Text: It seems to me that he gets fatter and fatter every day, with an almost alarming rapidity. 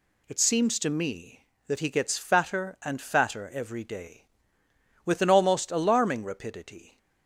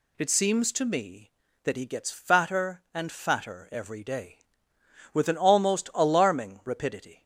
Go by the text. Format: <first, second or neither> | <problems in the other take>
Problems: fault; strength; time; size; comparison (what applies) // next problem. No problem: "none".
neither | none